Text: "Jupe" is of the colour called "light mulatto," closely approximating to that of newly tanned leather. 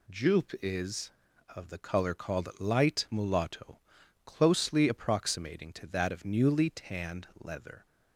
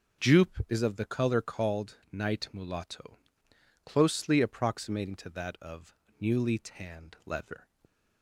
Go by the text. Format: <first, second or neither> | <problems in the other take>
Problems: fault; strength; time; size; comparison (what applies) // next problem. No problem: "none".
first | says "night" for "light"; at 2.1 s // pauses between "of" and "newly"; slight; at 5.9 s; 0.24 s long